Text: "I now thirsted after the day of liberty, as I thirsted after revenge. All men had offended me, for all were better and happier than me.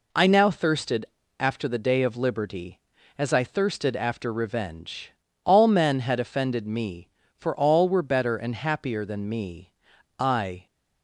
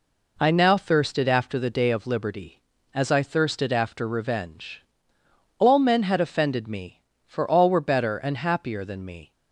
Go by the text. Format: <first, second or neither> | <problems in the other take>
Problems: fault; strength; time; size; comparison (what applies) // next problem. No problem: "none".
second | pauses between "thirsted" and "after"; slight; at 1.0 s; 0.32 s long // goes on to say "I"; slight; from 10.1 s on; 0.48 s long